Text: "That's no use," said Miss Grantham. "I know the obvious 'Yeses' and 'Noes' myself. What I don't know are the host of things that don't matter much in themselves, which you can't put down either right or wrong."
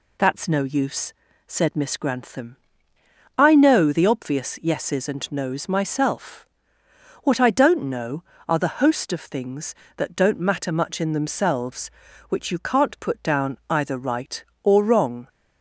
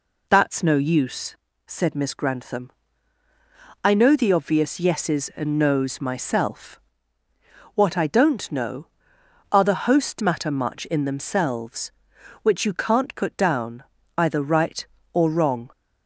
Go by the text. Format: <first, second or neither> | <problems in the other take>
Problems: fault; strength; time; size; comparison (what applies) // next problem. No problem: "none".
first | skips "of things that don't"; at 10.2 s // pauses between "down" and "either"; slight; at 13.8 s; 0.32 s long